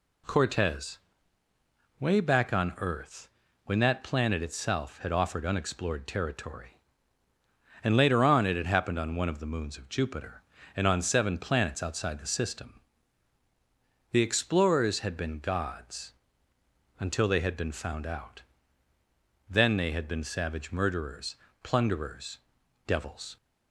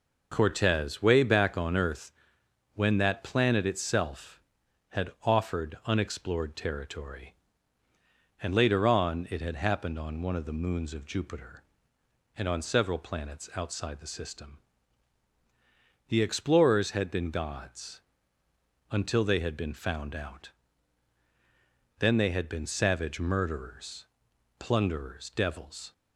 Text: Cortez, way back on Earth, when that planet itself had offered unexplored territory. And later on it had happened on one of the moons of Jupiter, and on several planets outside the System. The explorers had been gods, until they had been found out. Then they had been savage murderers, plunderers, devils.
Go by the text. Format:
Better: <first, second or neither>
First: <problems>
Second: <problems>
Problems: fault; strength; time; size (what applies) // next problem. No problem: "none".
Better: second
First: says "seven" for "several"; at 11.0 s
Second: none